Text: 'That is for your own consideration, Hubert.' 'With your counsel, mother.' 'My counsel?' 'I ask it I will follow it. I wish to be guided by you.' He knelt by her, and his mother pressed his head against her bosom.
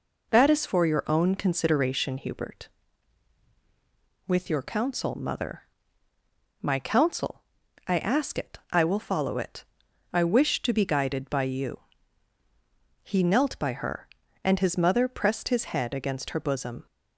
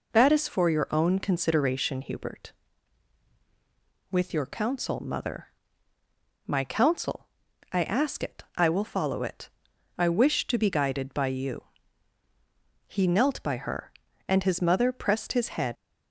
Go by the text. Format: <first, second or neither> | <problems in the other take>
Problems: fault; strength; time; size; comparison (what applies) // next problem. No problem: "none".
first | stops before "against her bosom"; at 15.7 s